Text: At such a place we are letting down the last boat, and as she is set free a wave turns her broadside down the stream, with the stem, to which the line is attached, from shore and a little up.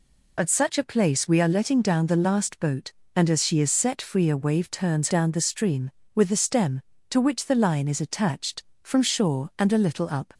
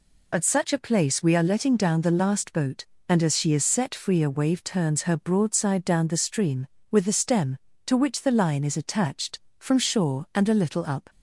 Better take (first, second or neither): second